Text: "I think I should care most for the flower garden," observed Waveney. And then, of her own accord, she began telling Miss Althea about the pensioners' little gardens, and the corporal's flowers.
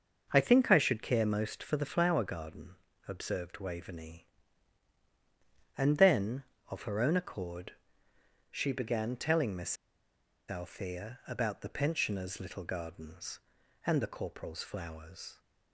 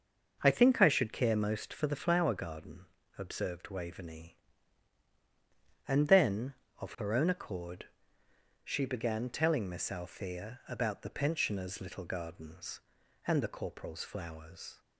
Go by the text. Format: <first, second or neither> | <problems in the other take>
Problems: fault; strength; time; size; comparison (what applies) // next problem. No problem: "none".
second | starts louder than the rest; until 1.3 s; 6 dB; also in the second // pauses between "Miss" and "Althea"; noticeable; at 9.7 s; 0.75 s long